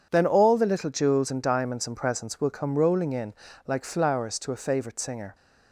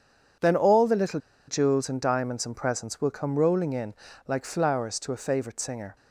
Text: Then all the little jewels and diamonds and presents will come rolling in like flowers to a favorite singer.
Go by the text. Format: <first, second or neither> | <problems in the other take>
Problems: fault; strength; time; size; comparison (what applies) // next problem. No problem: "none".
first | pauses between "little" and "jewels"; slight; at 1.1 s; 0.29 s long // pauses between "in" and "like"; slight; at 3.9 s; 0.34 s long; slight in the first